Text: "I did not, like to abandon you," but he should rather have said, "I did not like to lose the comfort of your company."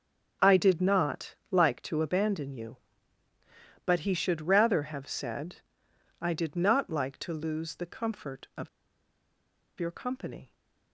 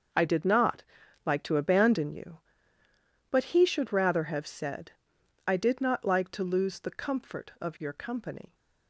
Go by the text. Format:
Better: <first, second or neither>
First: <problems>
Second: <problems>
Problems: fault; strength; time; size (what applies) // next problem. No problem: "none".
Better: second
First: starts louder than the rest; until 1.5 s; 7 dB // pauses between "of" and "your"; at 8.6 s; 1.1 s long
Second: starts louder than the rest; until 1.5 s; 6.5 dB